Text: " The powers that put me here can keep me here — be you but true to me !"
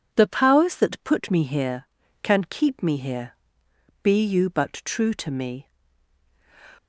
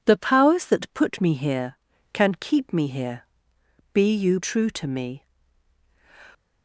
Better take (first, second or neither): first